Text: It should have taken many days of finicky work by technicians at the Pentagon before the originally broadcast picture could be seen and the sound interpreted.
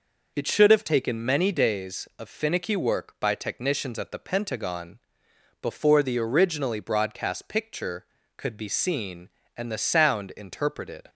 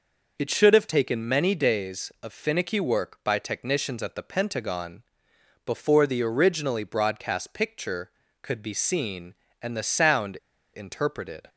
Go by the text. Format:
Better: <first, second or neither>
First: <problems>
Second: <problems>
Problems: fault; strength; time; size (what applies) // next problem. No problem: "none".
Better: first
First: pauses between "Pentagon" and "before"; noticeable; at 4.9 s; 0.62 s long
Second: pauses between "Pentagon" and "before"; noticeable; at 5.0 s; 0.62 s long // pauses between "sound" and "interpreted"; at 10.3 s; 0.37 s long